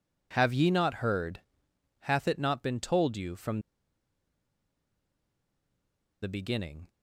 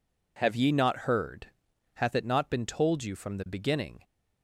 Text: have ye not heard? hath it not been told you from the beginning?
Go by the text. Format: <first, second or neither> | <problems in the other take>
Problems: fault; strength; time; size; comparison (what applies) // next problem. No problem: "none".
second | pauses between "from" and "the"; strong; at 3.5 s; 2.6 s long